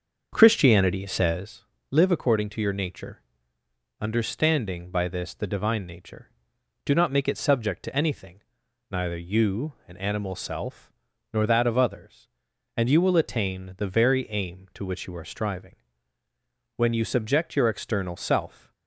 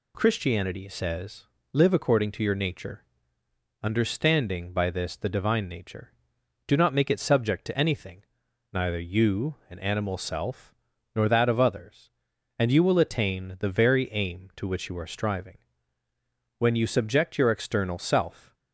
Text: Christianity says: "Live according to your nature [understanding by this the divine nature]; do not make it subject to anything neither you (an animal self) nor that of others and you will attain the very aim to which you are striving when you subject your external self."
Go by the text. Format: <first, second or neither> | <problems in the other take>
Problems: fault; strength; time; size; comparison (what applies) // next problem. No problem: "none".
second | starts louder than the rest; until 1.5 s; 6.5 dB // pauses between "nature" and "understanding"; noticeable; at 3.2 s; 0.78 s long; noticeable in the second // pauses between "anything" and "neither"; noticeable; at 8.4 s; 0.48 s long; noticeable in the second // pauses between "striving" and "when"; at 15.7 s; 1.0 s long; also in the second